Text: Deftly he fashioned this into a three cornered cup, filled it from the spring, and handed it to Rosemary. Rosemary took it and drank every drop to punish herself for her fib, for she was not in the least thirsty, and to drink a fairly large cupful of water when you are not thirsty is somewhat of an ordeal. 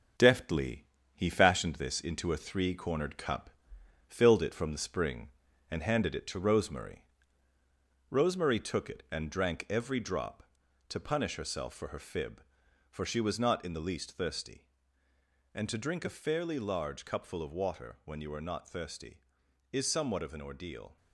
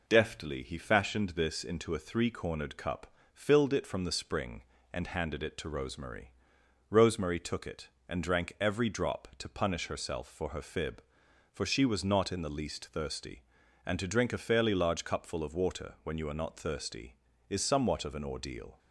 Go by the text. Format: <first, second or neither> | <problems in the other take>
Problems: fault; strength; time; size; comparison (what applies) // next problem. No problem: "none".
second | gets quieter; noticeable; throughout; 4.5 dB // pauses between "Deftly" and "he"; slight; at 0.8 s; 0.30 s long